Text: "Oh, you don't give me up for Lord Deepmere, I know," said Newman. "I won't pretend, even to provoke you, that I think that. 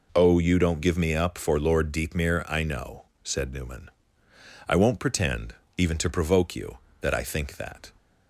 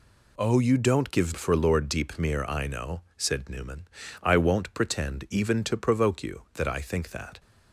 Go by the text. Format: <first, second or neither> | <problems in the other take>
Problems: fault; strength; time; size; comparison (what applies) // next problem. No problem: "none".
first | skips "me up"; at 1.3 s